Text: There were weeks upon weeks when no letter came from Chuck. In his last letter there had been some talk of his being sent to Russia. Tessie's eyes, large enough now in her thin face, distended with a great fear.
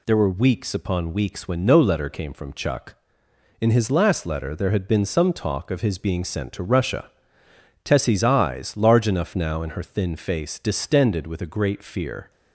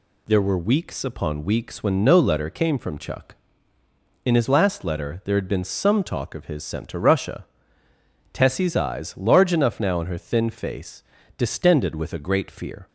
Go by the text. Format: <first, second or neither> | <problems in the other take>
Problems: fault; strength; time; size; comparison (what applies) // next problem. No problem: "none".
first | skips "being"; at 6.6 s